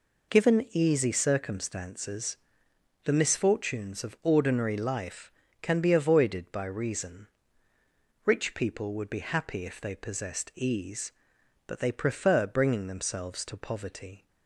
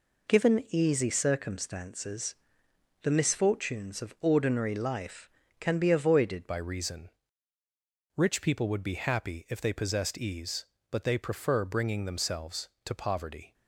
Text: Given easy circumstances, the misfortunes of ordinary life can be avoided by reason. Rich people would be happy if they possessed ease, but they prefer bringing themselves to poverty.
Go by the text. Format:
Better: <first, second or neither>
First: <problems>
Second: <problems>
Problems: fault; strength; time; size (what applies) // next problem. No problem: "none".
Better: first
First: none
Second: changes voice at "by"; from 6.4 s on; 7.1 s long